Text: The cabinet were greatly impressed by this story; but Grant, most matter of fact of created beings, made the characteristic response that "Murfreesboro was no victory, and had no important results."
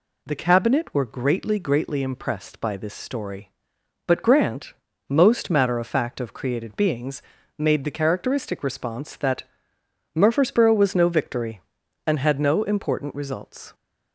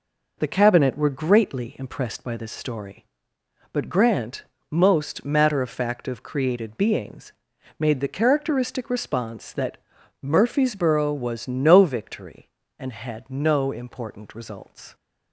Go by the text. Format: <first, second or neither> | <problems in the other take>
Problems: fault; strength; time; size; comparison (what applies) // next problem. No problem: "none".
second | says "greatly" twice; at 1.5 s // pauses between "that" and "Murfreesboro"; noticeable; at 9.4 s; 0.72 s long; also in the second